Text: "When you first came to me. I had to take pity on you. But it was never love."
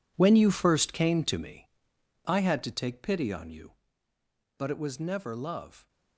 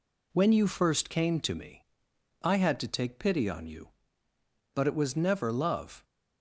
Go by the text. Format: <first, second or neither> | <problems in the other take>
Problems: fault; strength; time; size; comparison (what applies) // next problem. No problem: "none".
second | gets quieter; strong; throughout; 12.5 dB